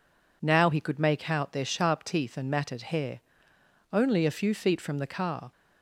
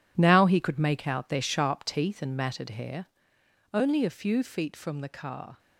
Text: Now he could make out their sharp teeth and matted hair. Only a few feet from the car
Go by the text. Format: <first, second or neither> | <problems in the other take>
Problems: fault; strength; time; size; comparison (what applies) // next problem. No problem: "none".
first | gets quieter; strong; throughout; 11 dB